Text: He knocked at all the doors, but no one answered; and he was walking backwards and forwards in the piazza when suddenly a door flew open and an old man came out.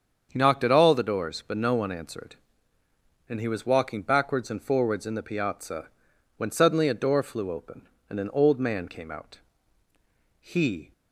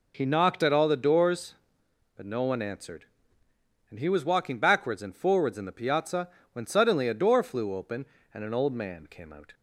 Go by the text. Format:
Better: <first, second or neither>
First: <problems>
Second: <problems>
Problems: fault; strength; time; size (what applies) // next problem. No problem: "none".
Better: second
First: starts louder than the rest; strong; until 1.3 s; 7 dB // pauses between "piazza" and "when"; noticeable; at 5.8 s; 0.50 s long // goes on to say "He"; from 10.3 s on; 0.54 s long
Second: pauses between "piazza" and "when"; slight; at 6.2 s; 0.24 s long